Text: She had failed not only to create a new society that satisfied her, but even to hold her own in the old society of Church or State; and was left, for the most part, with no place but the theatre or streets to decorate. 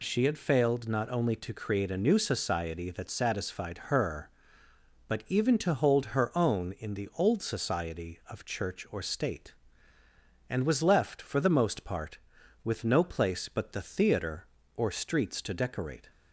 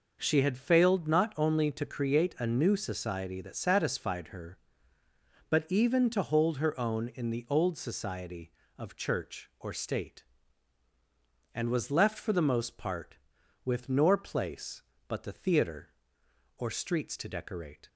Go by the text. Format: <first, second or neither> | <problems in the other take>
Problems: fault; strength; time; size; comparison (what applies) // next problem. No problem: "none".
first | says "nor" for "no"; at 13.8 s